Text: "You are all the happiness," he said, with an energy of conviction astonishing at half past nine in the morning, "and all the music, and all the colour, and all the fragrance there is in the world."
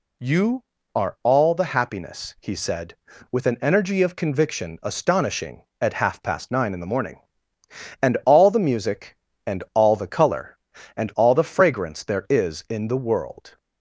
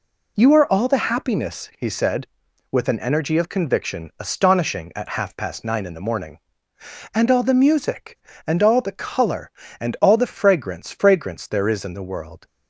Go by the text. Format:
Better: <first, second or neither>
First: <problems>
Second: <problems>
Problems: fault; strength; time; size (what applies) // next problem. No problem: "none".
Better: first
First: none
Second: says "fragrance" twice; at 10.9 s